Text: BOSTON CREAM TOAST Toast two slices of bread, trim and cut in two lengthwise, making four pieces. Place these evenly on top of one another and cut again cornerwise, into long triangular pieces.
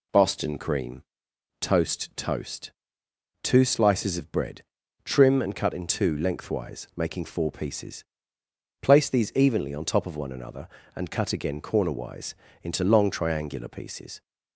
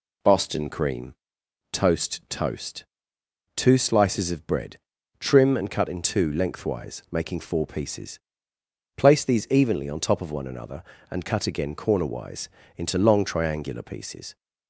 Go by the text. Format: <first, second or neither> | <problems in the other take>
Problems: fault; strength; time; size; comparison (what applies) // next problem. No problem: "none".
neither | pauses between "CREAM" and "TOAST"; noticeable; the same in both // pauses between "Toast" and "two"; noticeable; the same in both